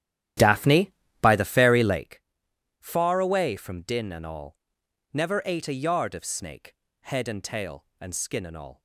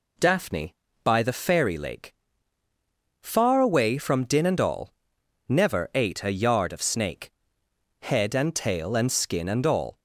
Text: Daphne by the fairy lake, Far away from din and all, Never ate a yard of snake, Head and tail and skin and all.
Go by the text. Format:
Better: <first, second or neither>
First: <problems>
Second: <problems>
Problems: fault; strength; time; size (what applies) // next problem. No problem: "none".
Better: second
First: starts louder than the rest; strong; until 2.1 s; 11.5 dB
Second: none